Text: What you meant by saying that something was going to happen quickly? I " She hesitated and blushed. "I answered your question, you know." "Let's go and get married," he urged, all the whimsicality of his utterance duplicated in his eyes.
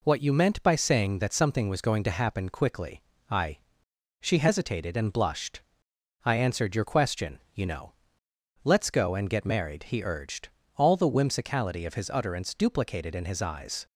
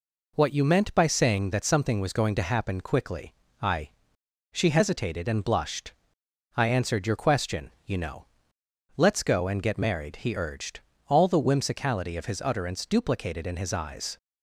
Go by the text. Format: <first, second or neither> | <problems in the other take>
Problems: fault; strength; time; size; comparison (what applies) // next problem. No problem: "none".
neither | none